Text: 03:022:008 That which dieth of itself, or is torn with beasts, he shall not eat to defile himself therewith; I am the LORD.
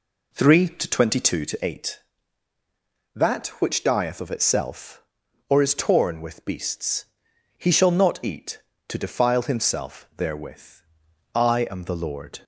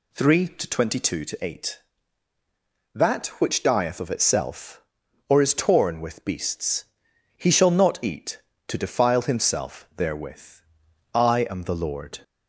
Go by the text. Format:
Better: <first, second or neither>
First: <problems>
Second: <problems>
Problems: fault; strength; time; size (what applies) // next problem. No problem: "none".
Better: second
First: starts louder than the rest; slight; until 1.9 s; 3 dB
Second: none